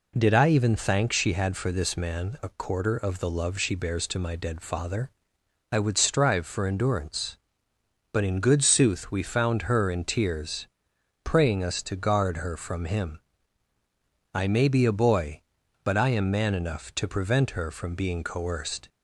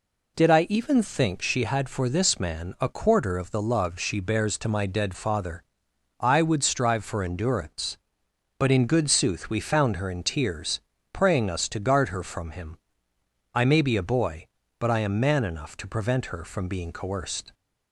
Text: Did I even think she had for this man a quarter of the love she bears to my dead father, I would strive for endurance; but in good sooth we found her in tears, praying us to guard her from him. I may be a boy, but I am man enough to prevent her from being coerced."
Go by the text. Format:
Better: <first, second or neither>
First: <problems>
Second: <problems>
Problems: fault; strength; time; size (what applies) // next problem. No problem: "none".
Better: second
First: says "thank" for "think"; at 0.7 s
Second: none